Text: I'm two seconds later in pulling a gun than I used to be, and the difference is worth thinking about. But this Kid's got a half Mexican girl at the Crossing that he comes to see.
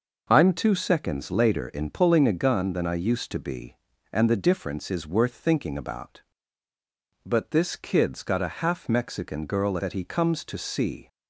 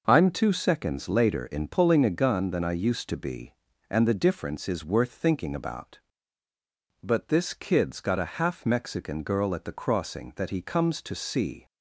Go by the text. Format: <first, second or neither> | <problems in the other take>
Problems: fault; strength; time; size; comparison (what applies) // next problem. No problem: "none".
second | skips "at the Crossing"; at 9.7 s